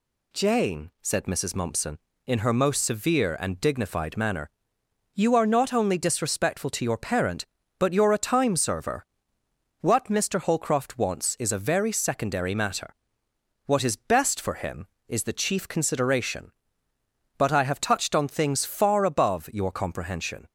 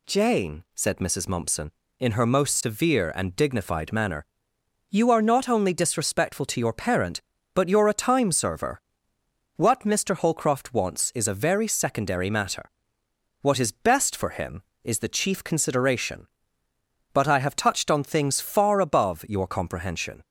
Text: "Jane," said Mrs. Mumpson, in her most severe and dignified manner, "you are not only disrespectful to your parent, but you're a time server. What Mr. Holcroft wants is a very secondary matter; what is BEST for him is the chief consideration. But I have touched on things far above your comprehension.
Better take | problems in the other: neither | none

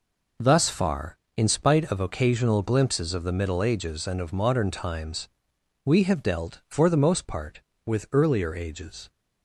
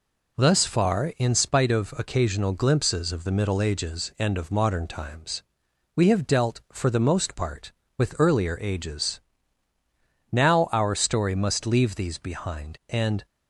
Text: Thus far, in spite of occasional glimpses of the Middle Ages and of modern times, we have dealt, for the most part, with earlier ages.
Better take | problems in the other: first | goes on to say "Now our story must leave these behind and"; strong; from 10.3 s on; 2.9 s long

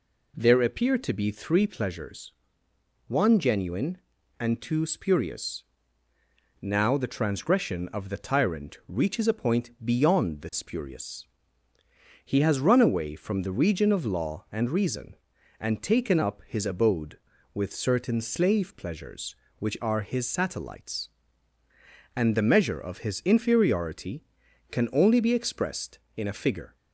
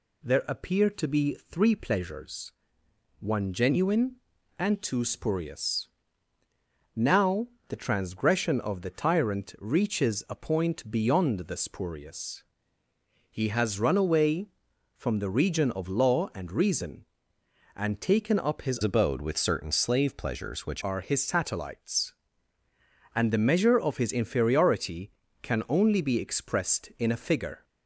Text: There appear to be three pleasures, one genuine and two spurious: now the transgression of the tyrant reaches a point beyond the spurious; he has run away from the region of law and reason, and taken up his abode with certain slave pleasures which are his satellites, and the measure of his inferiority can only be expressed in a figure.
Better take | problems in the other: first | pauses between "now" and "the"; slight; at 7.4 s; 0.22 s long // changes voice from "abode" to "which"; from 18.8 to 20.8 s; 2.0 s long

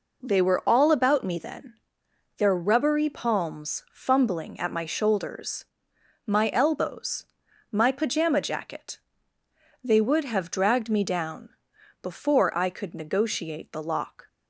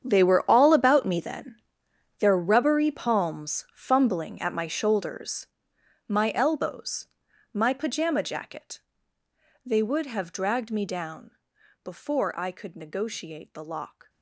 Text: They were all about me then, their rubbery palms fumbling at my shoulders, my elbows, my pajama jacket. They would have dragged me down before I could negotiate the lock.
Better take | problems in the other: first | gets quieter; strong; throughout; 15.5 dB // pauses between "down" and "before"; noticeable; at 11.3 s; 0.54 s long; noticeable in the first

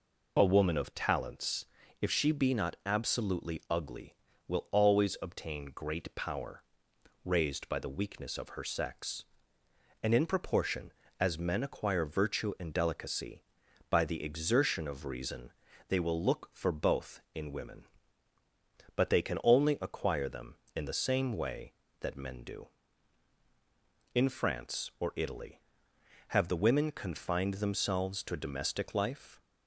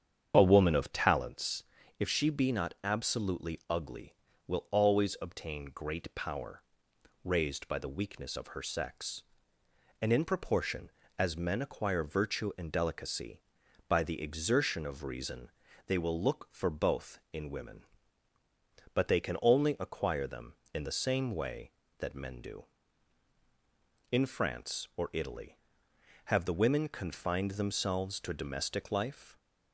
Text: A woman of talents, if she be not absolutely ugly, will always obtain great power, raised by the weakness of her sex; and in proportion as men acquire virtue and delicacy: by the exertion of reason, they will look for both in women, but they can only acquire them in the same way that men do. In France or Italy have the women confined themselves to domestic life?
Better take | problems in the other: first | starts louder than the rest; strong; until 1.3 s; 7.5 dB

